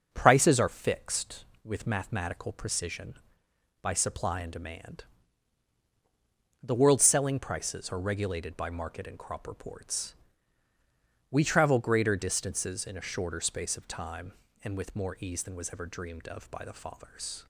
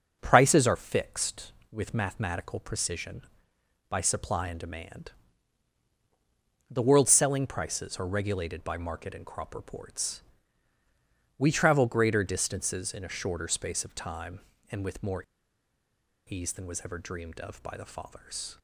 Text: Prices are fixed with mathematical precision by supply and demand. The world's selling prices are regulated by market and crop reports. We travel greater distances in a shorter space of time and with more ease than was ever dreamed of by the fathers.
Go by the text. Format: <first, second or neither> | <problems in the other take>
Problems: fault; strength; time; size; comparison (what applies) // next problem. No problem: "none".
first | starts louder than the rest; until 1.2 s; 6.5 dB; also in the first // pauses between "more" and "ease"; at 15.2 s; 1.0 s long